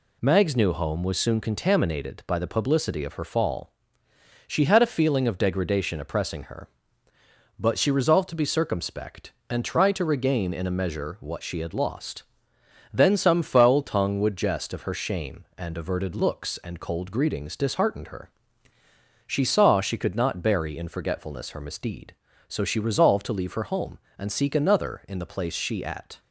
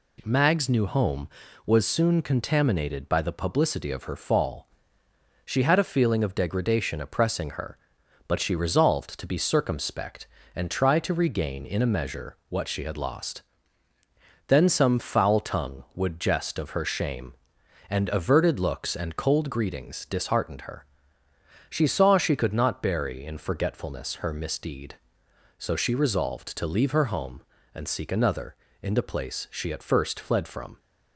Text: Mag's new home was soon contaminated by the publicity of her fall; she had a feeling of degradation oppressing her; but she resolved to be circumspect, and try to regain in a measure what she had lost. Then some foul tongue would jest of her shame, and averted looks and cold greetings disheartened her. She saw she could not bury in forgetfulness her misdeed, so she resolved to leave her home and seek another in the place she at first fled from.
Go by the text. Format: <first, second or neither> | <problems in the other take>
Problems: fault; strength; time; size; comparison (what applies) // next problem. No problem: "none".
second | stops before "first fled from"; at 26.2 s